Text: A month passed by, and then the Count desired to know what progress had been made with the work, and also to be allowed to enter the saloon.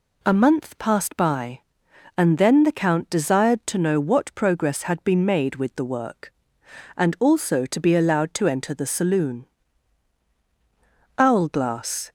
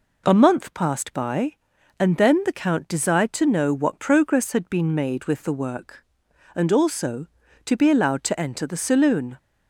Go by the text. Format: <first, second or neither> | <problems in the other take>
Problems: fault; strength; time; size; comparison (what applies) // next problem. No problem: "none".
second | goes on to say "Owlglass"; noticeable; from 11.1 s on; 0.94 s long